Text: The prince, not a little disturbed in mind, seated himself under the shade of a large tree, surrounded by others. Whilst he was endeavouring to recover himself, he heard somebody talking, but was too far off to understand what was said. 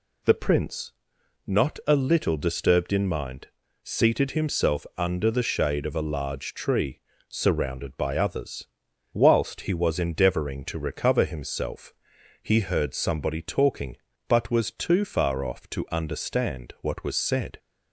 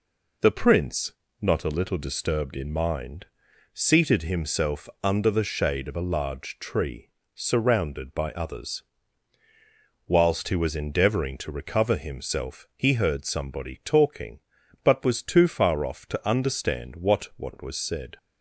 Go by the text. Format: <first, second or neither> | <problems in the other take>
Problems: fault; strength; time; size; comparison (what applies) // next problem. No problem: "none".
first | pauses between "himself" and "under"; slight; at 4.8 s; 0.16 s long // says "what" twice; at 17.3 s